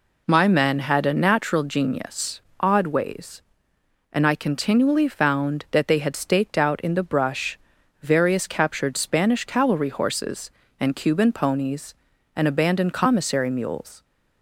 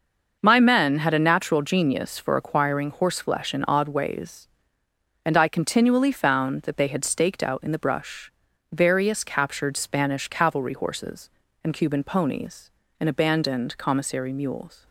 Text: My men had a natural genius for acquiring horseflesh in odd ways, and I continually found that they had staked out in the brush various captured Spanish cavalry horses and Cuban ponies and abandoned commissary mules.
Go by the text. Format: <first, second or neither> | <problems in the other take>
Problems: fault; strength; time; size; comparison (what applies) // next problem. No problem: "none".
second | skips "for acquiring horseflesh in"; at 2.5 s // pauses between "brush" and "various"; at 7.5 s; 0.44 s long; also in the second